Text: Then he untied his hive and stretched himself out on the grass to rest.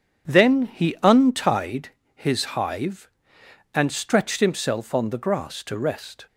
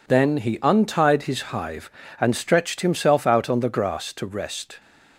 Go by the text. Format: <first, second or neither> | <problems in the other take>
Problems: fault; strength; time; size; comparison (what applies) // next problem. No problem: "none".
second | starts louder than the rest; strong; until 1.3 s; 8 dB // pauses between "untied" and "his"; slight; at 1.9 s; 0.26 s long // skips "out"; at 4.9 s